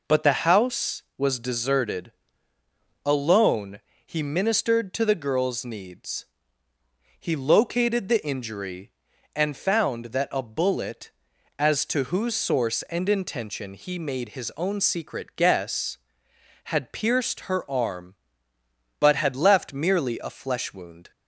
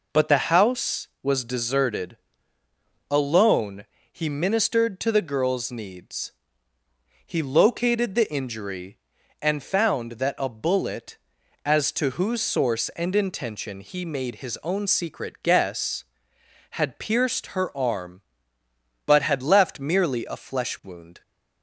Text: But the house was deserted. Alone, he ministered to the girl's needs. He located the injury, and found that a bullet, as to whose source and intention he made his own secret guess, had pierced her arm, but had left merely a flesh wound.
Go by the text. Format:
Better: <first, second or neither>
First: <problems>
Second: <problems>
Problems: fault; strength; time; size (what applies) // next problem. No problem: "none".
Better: neither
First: none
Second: none